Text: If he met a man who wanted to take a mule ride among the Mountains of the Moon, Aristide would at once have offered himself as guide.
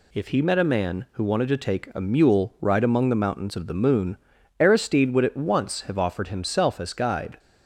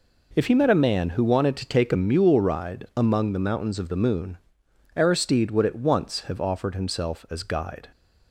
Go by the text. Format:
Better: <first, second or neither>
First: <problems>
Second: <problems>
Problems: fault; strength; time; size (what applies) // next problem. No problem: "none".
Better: neither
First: none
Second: none